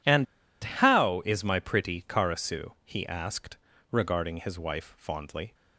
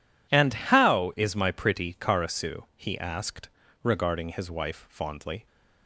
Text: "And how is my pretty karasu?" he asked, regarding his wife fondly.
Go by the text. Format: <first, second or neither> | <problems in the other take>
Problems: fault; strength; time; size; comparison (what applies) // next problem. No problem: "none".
second | pauses between "And" and "how"; at 0.2 s; 0.36 s long